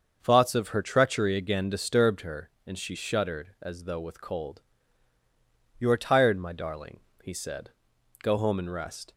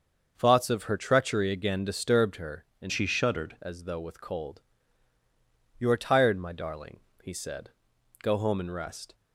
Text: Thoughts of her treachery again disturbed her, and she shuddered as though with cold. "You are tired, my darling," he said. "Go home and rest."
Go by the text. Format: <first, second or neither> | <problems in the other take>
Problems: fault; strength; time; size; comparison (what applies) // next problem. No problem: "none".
first | starts louder than the rest; until 1.3 s; 6.5 dB; also in the first // changes voice from "she" to "shuddered"; from 2.8 to 3.5 s; 0.7 s long